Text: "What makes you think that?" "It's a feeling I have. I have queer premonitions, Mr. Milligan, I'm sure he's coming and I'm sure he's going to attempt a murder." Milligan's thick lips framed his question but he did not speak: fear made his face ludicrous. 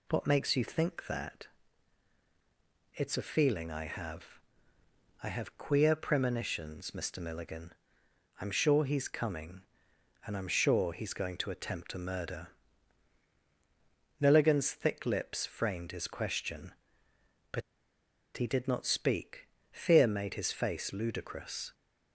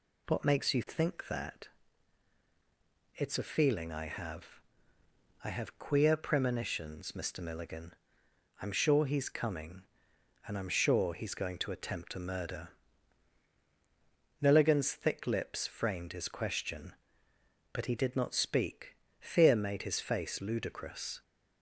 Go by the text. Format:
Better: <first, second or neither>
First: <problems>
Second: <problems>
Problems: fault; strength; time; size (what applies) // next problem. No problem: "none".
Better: second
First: pauses between "but" and "he"; noticeable; at 17.6 s; 0.75 s long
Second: none